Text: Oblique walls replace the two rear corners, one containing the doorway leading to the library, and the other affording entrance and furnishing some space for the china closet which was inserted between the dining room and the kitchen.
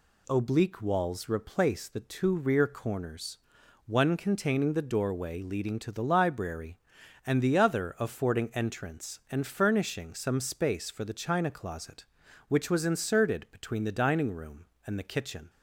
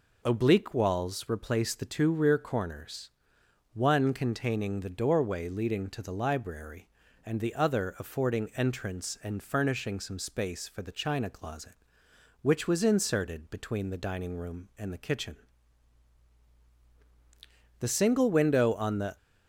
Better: first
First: none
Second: goes on to say "The single window on the"; from 17.7 s on; 1.3 s long

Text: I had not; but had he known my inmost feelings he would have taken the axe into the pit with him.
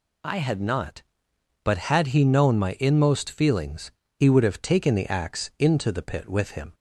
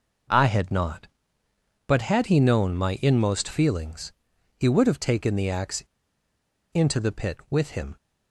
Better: first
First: pauses between "feelings" and "he"; slight; at 3.9 s; 0.25 s long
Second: pauses between "feelings" and "he"; noticeable; at 4.1 s; 0.46 s long // pauses between "axe" and "into"; noticeable; at 5.8 s; 0.91 s long

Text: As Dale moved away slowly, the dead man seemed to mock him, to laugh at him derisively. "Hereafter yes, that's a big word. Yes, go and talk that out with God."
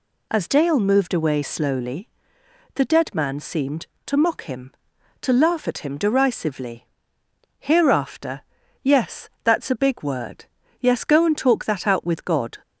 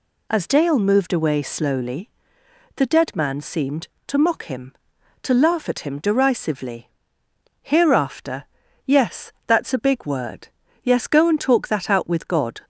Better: neither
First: pauses between "Hereafter" and "yes"; at 8.4 s; 0.42 s long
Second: pauses between "Hereafter" and "yes"; at 8.4 s; 0.42 s long

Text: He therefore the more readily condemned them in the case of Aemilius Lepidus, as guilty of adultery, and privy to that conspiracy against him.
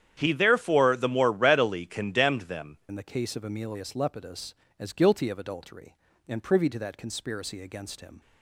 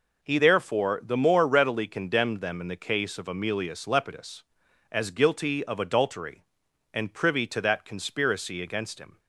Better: second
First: starts louder than the rest; strong; until 1.1 s; 9.5 dB // changes voice at "in"; from 2.8 s on; 5.4 s long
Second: none

